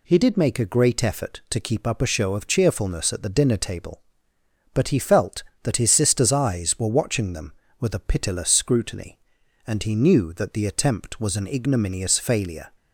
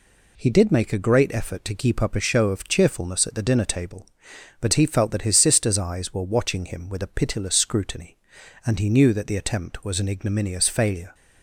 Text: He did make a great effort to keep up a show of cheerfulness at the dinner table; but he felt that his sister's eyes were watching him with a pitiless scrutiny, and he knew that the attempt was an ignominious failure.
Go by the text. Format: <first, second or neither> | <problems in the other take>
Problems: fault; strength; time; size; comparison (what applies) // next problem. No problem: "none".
second | says "them" for "him"; at 7.3 s